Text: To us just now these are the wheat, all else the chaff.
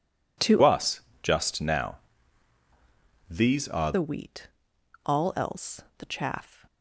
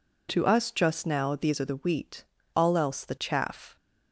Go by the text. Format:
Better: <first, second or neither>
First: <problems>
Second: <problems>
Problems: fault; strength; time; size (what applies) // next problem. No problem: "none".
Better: second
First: changes voice from "us" to "are"; from 0.6 to 3.9 s; 3.3 s long // pauses between "us" and "just"; slight; at 0.9 s; 0.22 s long // pauses between "now" and "these"; strong; at 1.9 s; 1.3 s long // pauses between "else" and "the"; slight; at 5.8 s; 0.16 s long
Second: none